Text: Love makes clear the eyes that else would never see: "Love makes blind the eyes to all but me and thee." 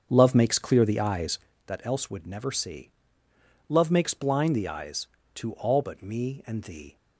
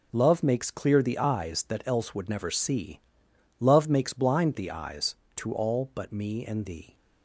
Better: second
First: starts louder than the rest; strong; until 1.5 s; 7.5 dB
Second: none

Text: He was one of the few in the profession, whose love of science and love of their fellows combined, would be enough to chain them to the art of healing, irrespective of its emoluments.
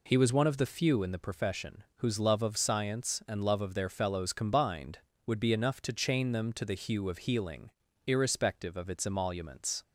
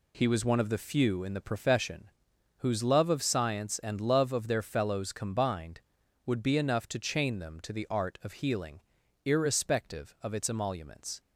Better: second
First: says "hue" for "art"; at 6.7 s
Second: none

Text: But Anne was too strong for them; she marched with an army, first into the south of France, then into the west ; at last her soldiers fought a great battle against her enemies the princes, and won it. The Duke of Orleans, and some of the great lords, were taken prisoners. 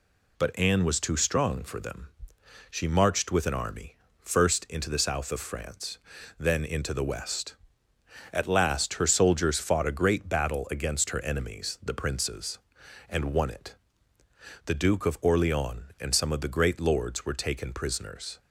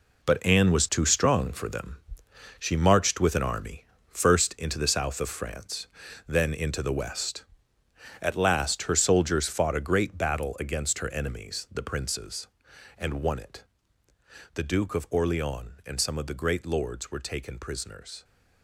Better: first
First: none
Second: gets quieter; strong; throughout; 10 dB

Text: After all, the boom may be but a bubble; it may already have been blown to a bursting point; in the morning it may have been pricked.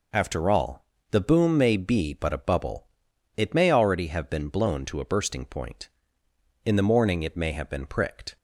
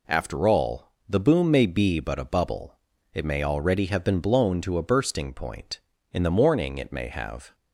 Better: first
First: none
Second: stops before "been pricked"; at 7.5 s

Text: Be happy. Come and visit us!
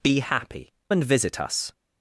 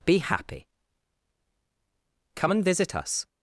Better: second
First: skips "Come"; at 0.8 s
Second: none

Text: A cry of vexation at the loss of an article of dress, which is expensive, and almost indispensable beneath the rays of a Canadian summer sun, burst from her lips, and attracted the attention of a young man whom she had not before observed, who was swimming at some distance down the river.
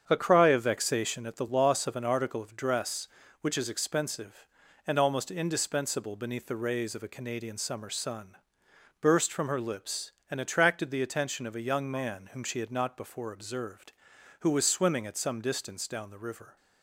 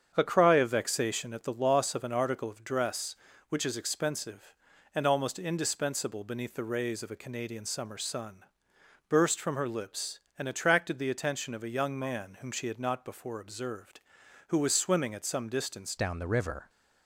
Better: first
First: starts louder than the rest; strong; until 1.1 s; 7.5 dB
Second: starts louder than the rest; strong; until 1.1 s; 7.5 dB // changes voice at "down"; from 15.9 s on; 0.7 s long

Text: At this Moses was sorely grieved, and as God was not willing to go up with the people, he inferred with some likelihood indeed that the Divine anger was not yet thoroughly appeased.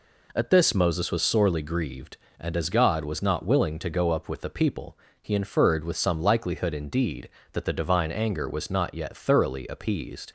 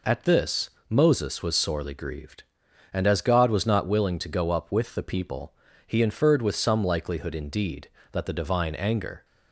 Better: first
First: none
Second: pauses between "this" and "Moses"; slight; at 0.6 s; 0.20 s long // stops before "was not yet thoroughly appeased"; at 9.2 s

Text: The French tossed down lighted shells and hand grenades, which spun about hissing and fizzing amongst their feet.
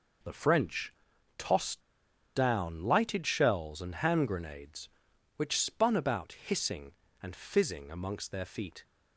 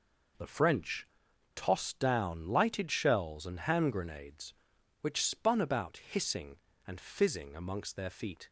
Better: second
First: pauses between "French" and "tossed"; noticeable; at 0.9 s; 0.46 s long // pauses between "tossed" and "down"; noticeable; at 1.8 s; 0.53 s long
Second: pauses between "French" and "tossed"; noticeable; at 1.0 s; 0.49 s long

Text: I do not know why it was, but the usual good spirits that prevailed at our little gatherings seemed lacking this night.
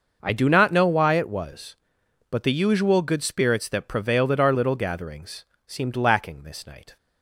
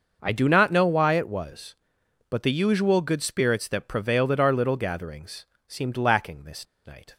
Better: first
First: starts louder than the rest; until 1.2 s; 6 dB // pauses between "gatherings" and "seemed"; slight; at 5.4 s; 0.22 s long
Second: starts louder than the rest; until 1.2 s; 6 dB // pauses between "gatherings" and "seemed"; slight; at 5.4 s; 0.22 s long // pauses between "this" and "night"; slight; at 6.6 s; 0.20 s long

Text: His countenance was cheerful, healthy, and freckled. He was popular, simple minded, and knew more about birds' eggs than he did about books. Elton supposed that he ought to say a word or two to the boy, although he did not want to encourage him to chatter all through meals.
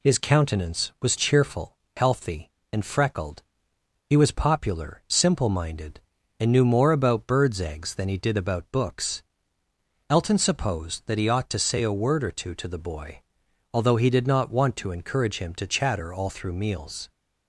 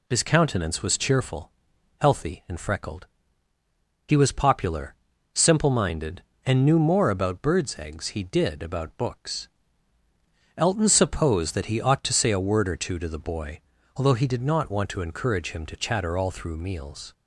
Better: first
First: none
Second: skips "than"; at 8.0 s

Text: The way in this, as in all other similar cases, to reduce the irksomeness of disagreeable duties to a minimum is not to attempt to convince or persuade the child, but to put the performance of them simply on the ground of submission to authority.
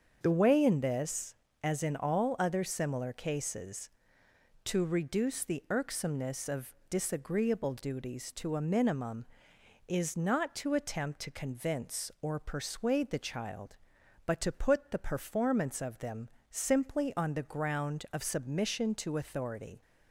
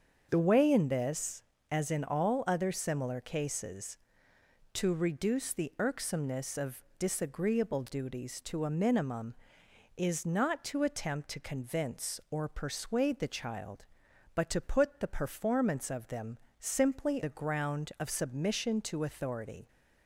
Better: first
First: starts louder than the rest; until 1.2 s; 7 dB // pauses between "of" and "disagreeable"; slight; at 6.7 s; 0.16 s long // pauses between "them" and "simply"; slight; at 16.2 s; 0.22 s long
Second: starts louder than the rest; until 1.3 s; 7 dB // pauses between "of" and "disagreeable"; slight; at 6.8 s; 0.16 s long // pauses between "them" and "simply"; slight; at 16.3 s; 0.22 s long // skips "on"; at 17.2 s

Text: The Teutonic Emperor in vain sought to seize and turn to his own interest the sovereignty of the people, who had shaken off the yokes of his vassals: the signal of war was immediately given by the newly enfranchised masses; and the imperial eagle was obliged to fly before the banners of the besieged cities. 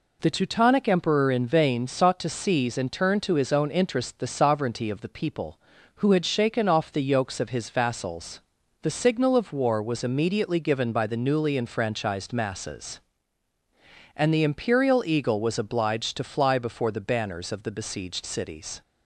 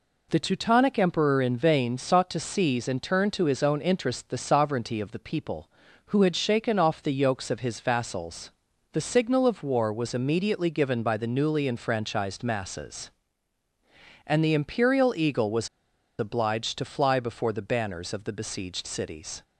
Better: first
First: none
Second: pauses between "was" and "obliged"; noticeable; at 15.6 s; 0.52 s long

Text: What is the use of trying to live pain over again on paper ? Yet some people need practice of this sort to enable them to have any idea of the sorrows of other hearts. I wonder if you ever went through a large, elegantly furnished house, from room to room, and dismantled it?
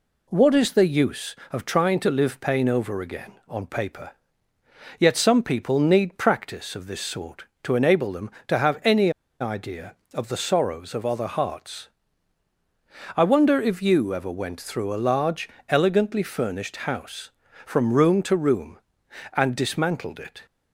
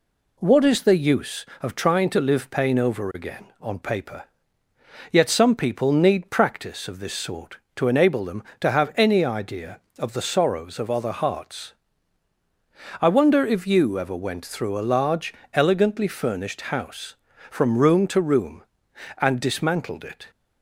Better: second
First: pauses between "any" and "idea"; slight; at 9.0 s; 0.30 s long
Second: none

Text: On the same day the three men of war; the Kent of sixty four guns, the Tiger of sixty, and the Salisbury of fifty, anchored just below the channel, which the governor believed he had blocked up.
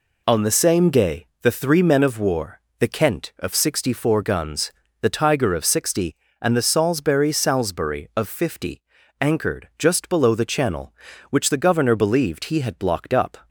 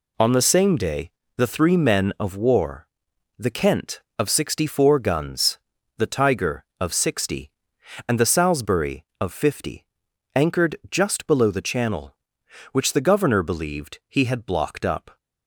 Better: second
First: pauses between "day" and "the"; slight; at 1.2 s; 0.16 s long // says "Salisbury" twice; at 7.3 s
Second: pauses between "day" and "the"; slight; at 1.1 s; 0.26 s long

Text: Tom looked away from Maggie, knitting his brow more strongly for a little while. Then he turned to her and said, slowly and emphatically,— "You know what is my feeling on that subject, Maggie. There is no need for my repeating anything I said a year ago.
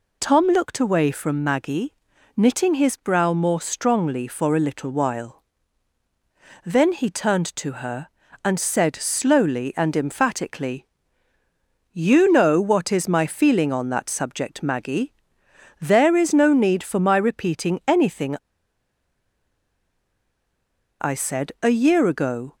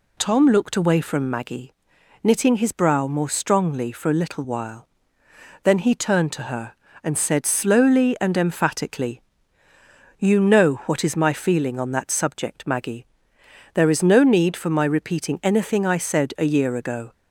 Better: second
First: pauses between "anything" and "I"; strong; at 18.3 s; 2.6 s long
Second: none

